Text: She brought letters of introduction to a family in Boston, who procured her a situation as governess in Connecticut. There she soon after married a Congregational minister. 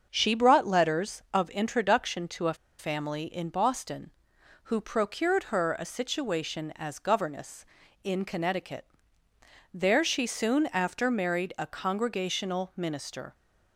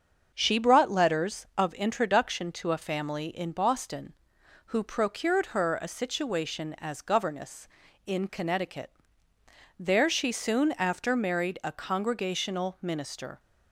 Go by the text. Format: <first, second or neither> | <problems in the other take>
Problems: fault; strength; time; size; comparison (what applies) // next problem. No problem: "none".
second | starts louder than the rest; until 1.1 s; 6.5 dB; also in the second // pauses between "a" and "family"; slight; at 2.5 s; 0.24 s long